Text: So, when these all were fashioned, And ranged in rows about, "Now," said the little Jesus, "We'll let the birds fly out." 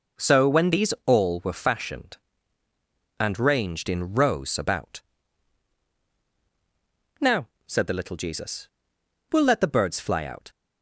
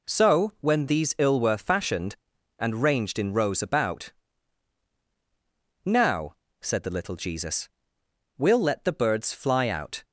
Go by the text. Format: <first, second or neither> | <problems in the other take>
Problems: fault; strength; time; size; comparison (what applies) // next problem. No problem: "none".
first | says "ill" for "all"; at 1.1 s